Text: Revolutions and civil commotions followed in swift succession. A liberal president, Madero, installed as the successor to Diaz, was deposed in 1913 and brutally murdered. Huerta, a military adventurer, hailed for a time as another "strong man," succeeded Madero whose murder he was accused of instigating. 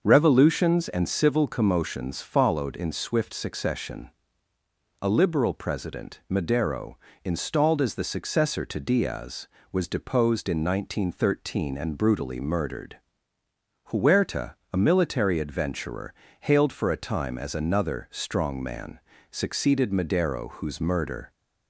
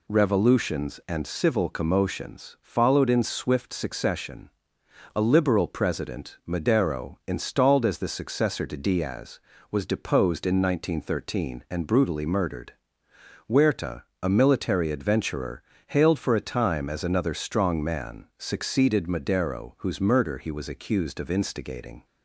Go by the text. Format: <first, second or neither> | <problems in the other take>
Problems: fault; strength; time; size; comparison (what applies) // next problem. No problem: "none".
second | starts louder than the rest; until 1.0 s; 6.5 dB // stops before "he was accused of instigating"; at 21.3 s